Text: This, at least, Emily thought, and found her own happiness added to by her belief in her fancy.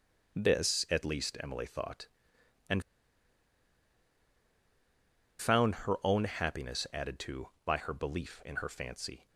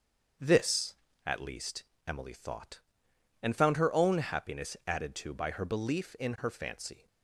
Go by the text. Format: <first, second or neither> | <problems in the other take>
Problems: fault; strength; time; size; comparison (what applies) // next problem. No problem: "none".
second | starts louder than the rest; until 1.4 s; 6 dB; also in the second // pauses between "and" and "found"; strong; at 2.8 s; 2.5 s long